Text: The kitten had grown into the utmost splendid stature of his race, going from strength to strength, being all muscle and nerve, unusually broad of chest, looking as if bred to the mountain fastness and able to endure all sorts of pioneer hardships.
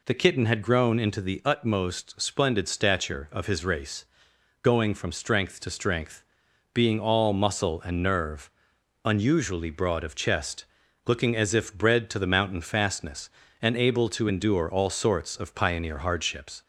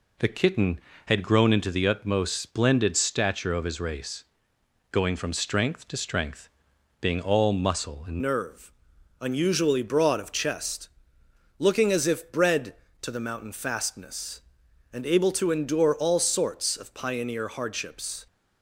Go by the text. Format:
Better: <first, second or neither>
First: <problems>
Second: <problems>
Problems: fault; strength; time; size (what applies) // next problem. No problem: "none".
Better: first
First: none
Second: changes voice at "nerve"; from 8.2 s on; 10.0 s long